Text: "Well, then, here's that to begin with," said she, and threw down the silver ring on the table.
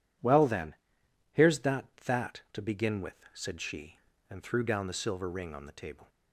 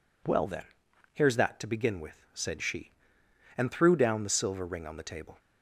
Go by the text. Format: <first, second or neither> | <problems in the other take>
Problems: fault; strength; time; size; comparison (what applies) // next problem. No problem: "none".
second | says "that" twice; at 2.0 s